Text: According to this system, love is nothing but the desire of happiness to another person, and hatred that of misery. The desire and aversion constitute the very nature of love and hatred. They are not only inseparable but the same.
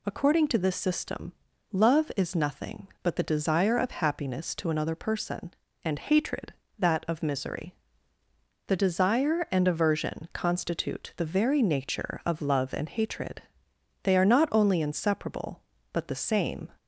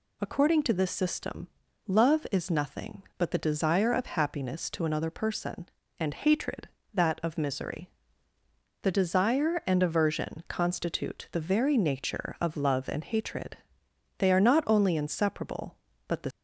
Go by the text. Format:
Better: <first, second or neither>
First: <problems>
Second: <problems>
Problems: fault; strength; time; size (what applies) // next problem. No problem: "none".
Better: first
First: none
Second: stops before "same"; at 16.3 s